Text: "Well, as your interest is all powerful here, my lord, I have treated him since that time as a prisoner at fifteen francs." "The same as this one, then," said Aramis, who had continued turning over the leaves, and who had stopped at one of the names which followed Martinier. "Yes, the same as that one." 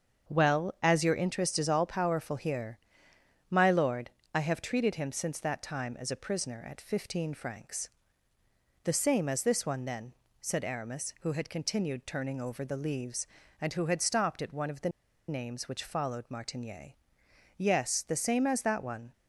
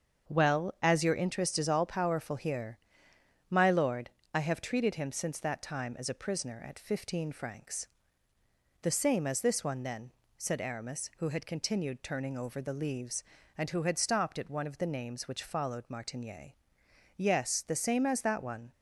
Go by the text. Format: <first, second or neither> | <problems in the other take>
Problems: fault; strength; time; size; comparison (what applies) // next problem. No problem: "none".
second | starts louder than the rest; until 1.3 s; 7 dB; also in the second // pauses between "the" and "names"; at 14.8 s; 0.39 s long